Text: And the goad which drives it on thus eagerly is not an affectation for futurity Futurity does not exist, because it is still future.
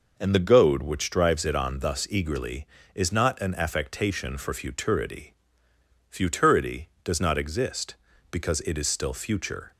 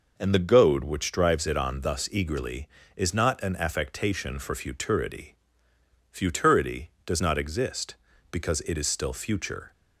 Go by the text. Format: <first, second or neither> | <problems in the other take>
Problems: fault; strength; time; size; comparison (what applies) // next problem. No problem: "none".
neither | pauses between "futurity" and "Futurity"; noticeable; the same in both